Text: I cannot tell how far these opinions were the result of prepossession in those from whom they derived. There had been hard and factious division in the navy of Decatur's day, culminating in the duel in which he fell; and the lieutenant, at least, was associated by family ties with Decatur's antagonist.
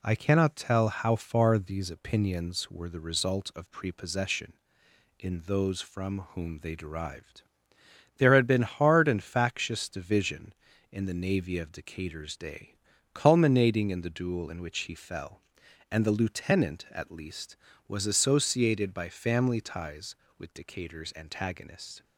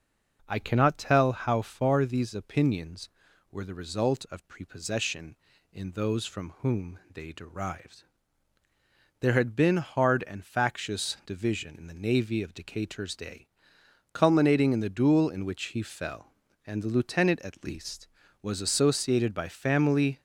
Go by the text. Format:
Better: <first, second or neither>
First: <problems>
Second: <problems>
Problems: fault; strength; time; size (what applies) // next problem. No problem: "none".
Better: first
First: none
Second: stops before "ties with Decatur's antagonist"; at 20.1 s